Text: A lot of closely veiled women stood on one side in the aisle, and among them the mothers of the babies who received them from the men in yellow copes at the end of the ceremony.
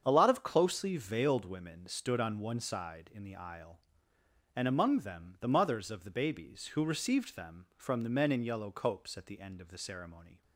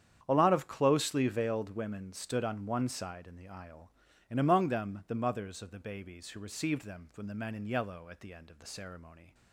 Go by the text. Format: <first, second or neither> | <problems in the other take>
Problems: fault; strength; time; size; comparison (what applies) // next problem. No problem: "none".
first | starts louder than the rest; strong; until 1.2 s; 9 dB; strong in the first // skips "copes"; at 8.0 s